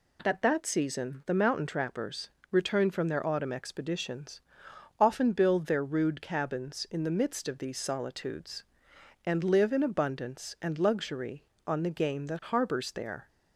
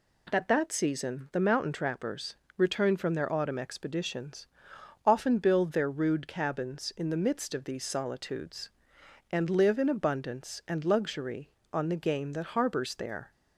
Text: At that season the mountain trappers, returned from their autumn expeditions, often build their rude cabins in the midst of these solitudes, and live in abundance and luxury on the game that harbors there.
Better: neither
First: none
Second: none

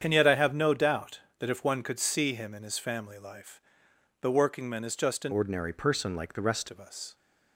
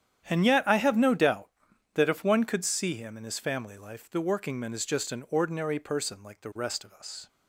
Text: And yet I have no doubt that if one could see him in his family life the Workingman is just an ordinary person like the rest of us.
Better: second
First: starts louder than the rest; strong; until 1.0 s; 8 dB // pauses between "life" and "the"; noticeable; at 3.6 s; 0.60 s long // changes voice from "ordinary" to "rest"; from 5.3 to 6.6 s; 1.3 s long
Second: starts louder than the rest; strong; until 1.3 s; 9.5 dB

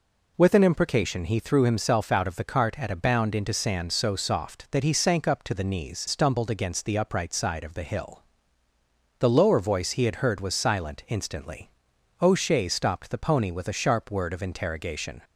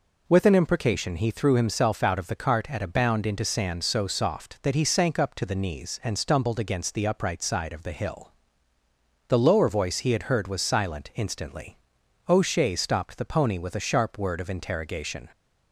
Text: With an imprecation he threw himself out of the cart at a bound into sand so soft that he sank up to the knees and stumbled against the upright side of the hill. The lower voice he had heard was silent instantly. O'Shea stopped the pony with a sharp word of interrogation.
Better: second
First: skips "and"; at 6.0 s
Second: none

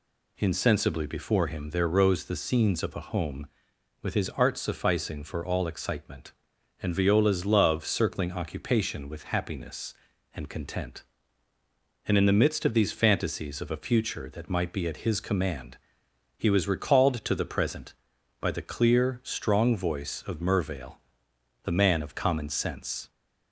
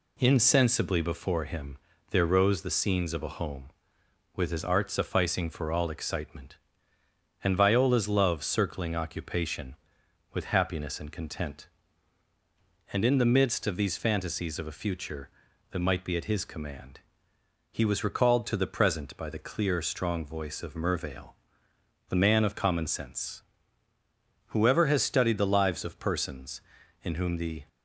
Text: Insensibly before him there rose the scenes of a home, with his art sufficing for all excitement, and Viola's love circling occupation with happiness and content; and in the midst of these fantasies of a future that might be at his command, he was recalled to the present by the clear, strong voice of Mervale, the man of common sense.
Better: first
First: none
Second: pauses between "him" and "there"; slight; at 1.7 s; 0.32 s long // goes on to say "Whoever has studied the lives of persons in whom the"; strong; from 24.4 s on; 3.2 s long

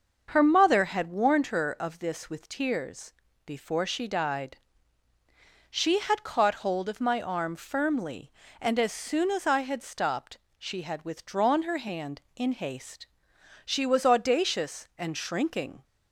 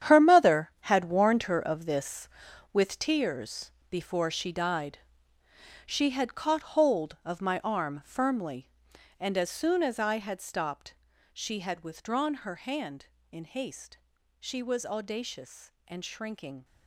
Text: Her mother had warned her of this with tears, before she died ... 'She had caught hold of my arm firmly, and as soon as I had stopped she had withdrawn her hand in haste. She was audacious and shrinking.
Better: first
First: starts louder than the rest; until 1.3 s; 6 dB // pauses between "stopped" and "she"; slight; at 10.3 s; 0.22 s long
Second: gets quieter; strong; throughout; 12.5 dB // starts louder than the rest; strong; until 1.2 s; 9.5 dB // pauses between "stopped" and "she"; at 10.9 s; 0.38 s long

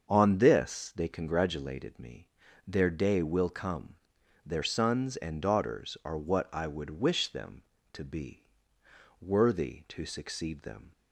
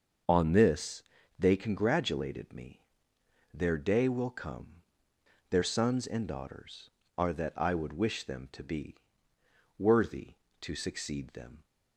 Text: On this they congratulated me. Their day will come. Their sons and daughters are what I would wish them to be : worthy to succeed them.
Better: first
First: starts louder than the rest; until 1.1 s; 6.5 dB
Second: starts louder than the rest; until 1.6 s; 6.5 dB // pauses between "this" and "they"; slight; at 1.0 s; 0.34 s long // says "that" for "what"; at 7.3 s

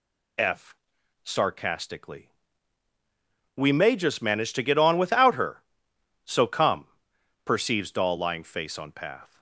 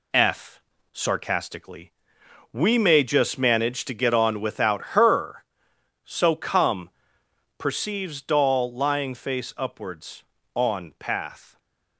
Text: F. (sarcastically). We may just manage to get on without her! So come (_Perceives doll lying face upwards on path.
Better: second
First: skips "upwards"; at 8.7 s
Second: none

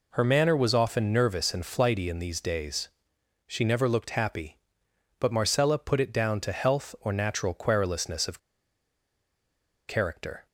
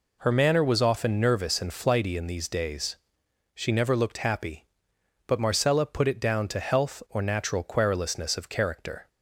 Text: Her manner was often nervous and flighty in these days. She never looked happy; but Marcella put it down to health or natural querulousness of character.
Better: second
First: pauses between "of" and "character"; strong; at 8.3 s; 1.4 s long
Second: none

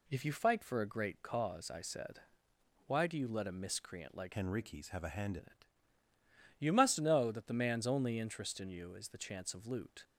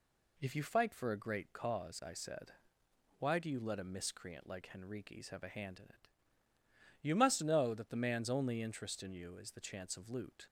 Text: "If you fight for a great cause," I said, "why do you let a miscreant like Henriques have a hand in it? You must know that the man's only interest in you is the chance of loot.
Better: second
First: changes voice from "Henriques" to "hand"; from 4.3 to 5.3 s; 1.0 s long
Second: none

